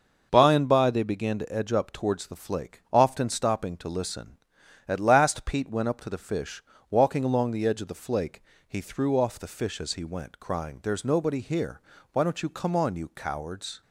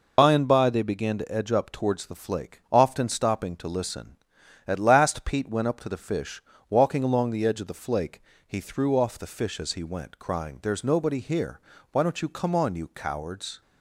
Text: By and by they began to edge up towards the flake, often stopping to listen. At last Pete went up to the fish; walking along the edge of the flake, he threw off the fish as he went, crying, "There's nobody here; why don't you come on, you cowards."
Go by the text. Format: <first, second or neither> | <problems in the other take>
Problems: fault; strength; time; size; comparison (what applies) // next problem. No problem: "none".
first | loses the start of "By"; at 0.1 s; 75 ms